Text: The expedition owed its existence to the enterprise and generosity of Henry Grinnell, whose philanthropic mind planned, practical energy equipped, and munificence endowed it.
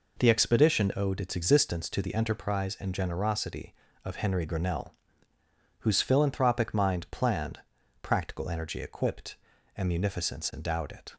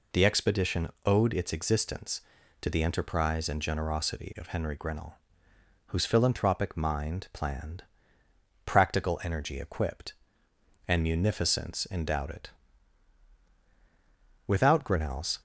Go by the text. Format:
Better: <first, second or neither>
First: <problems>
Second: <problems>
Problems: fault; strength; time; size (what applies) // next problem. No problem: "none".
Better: first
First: none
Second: pauses between "expedition" and "owed"; slight; at 0.8 s; 0.16 s long // goes on to say "Without Grinnell's"; noticeable; from 14.4 s on; 0.94 s long